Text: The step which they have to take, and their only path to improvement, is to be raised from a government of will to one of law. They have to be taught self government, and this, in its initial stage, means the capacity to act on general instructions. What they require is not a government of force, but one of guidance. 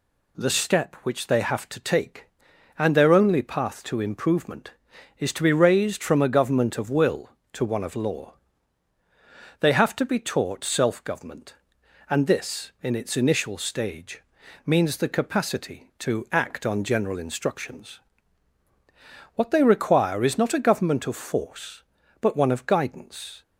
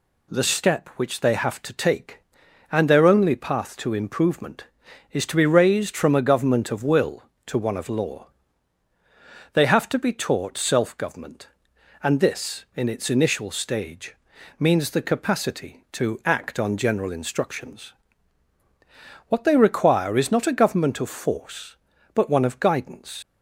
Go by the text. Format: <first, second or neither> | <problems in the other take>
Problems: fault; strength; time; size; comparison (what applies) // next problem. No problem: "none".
first | leaves "guidance" unfinished; at 23.2 s; 125 ms